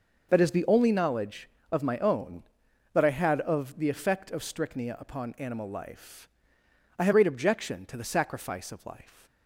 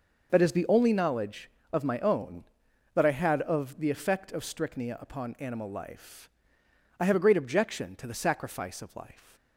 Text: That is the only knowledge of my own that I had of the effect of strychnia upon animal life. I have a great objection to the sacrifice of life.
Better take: second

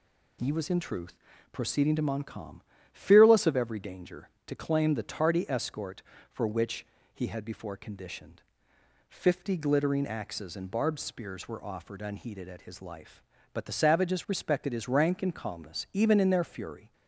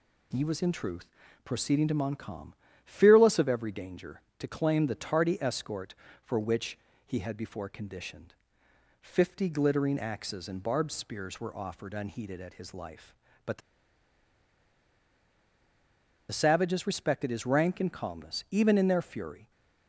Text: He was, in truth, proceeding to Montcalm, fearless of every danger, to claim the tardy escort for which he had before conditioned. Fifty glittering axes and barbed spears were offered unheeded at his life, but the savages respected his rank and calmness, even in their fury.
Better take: first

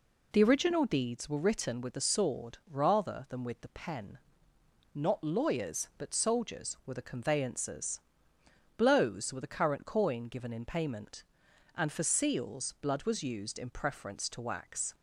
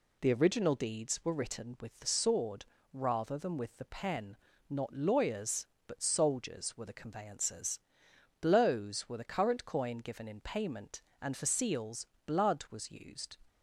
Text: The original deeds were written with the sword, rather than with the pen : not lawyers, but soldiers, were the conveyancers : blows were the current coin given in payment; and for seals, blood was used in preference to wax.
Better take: first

